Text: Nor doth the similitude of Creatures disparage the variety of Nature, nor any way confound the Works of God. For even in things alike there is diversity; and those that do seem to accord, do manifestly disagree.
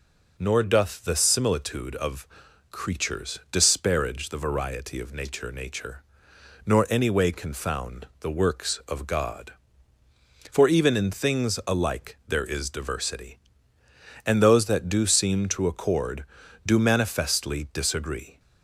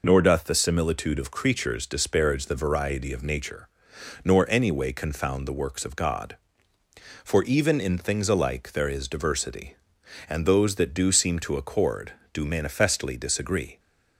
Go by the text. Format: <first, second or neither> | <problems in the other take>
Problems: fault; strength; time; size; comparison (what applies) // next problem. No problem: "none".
second | pauses between "of" and "Creatures"; at 2.2 s; 0.44 s long // says "Nature" twice; at 5.4 s